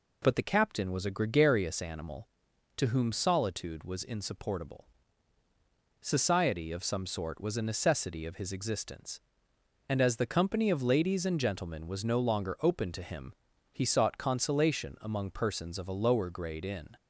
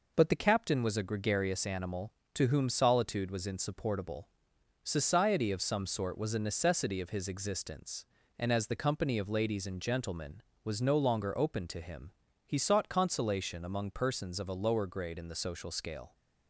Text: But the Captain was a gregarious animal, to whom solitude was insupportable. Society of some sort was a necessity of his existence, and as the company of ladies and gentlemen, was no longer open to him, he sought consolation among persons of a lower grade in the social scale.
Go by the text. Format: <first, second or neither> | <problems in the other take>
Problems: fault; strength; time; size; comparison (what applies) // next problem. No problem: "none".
second | stops before "the social scale"; at 16.9 s